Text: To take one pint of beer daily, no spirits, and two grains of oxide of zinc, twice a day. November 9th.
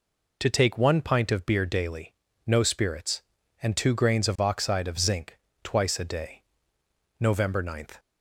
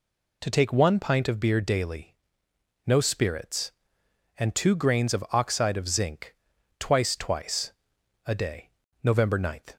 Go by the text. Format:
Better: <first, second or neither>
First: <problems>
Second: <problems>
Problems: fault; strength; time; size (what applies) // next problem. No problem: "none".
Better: first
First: none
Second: says "twice" twice; at 7.1 s